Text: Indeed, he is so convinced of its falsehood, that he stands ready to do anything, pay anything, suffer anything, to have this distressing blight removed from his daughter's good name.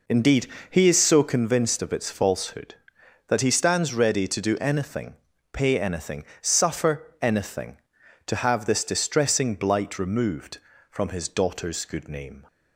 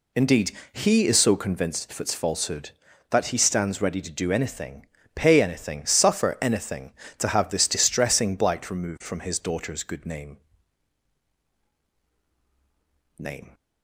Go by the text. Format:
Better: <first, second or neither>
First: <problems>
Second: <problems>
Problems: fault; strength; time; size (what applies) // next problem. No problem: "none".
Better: first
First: none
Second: says "name" twice; at 13.1 s